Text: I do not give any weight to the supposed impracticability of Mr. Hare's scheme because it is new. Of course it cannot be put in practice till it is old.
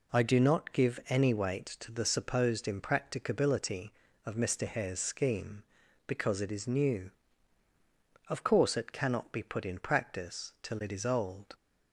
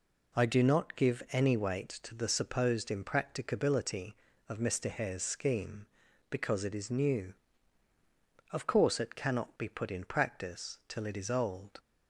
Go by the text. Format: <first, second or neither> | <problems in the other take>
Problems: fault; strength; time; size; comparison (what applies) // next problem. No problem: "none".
neither | none